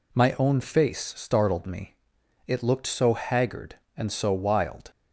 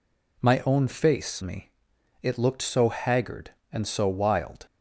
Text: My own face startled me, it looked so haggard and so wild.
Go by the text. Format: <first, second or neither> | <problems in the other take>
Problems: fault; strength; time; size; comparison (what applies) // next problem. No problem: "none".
first | skips "startled"; at 1.4 s